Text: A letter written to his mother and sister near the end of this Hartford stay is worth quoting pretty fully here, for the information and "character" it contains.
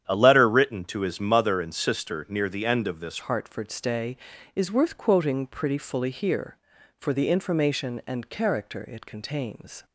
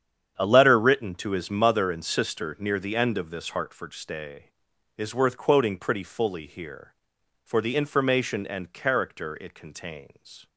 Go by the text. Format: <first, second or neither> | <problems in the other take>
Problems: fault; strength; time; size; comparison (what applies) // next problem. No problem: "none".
second | starts louder than the rest; strong; until 1.0 s; 9.5 dB; strong in the second // changes voice at "Hartford"; from 3.2 s on; 6.6 s long